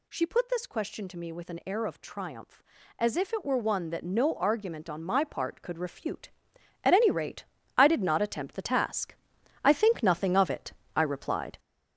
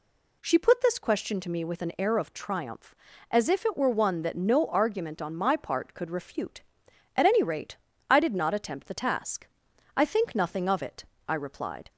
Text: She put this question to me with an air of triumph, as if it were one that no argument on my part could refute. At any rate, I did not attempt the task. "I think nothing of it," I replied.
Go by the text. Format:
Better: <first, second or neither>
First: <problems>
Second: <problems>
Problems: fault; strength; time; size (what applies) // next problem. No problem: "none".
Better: second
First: gets louder; noticeable; throughout; 5.5 dB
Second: none